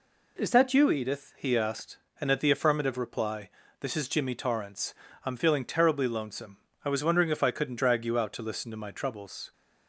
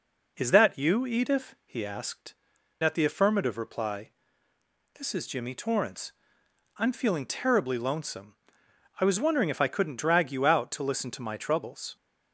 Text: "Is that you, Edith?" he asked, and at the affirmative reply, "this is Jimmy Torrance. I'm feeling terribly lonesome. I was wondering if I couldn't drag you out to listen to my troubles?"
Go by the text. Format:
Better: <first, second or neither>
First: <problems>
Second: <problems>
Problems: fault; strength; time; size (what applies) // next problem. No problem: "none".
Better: first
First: none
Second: skips "and"; at 2.5 s